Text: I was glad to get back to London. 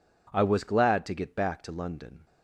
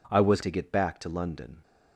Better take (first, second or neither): first